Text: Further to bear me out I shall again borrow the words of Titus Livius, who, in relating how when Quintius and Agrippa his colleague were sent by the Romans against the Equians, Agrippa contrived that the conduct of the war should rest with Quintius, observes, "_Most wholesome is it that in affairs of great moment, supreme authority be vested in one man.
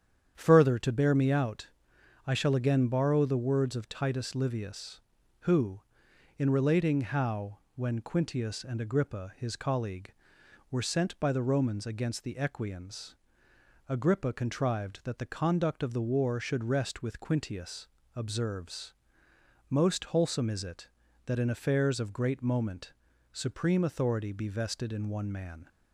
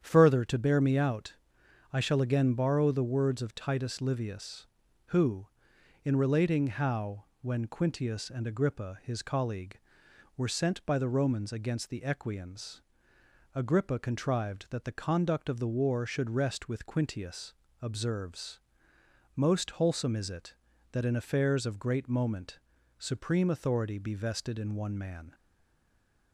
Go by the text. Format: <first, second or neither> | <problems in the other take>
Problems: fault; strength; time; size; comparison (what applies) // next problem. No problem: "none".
first | starts louder than the rest; strong; until 1.0 s; 9 dB; strong in the first // pauses between "out" and "I"; noticeable; at 1.3 s; 0.58 s long; noticeable in the first // pauses between "how" and "when"; slight; at 7.2 s; 0.18 s long; slight in the first // stays silent after the last word; from 25.3 s on; 1.0 s long